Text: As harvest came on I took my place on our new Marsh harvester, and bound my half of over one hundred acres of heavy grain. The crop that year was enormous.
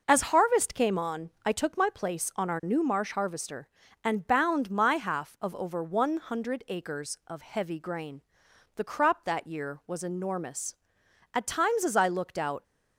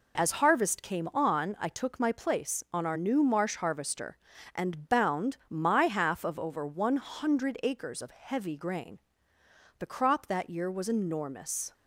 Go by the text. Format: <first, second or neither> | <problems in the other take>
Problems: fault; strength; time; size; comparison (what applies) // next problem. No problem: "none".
second | pauses between "on" and "I"; slight; at 1.2 s; 0.16 s long // goes on to say "At times as I looked out"; noticeable; from 11.3 s on; 1.3 s long